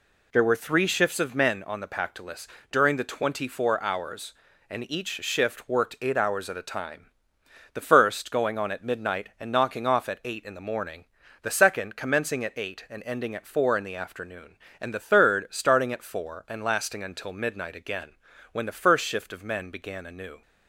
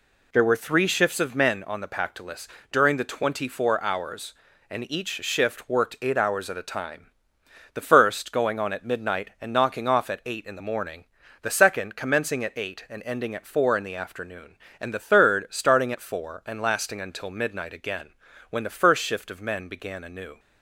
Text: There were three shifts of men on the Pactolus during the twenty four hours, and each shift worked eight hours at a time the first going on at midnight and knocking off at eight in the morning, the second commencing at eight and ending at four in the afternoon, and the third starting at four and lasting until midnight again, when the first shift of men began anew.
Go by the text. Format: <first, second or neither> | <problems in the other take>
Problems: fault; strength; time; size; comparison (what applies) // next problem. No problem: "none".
neither | pauses between "Pactolus" and "during"; slight; the same in both // pauses between "time" and "the"; noticeable; the same in both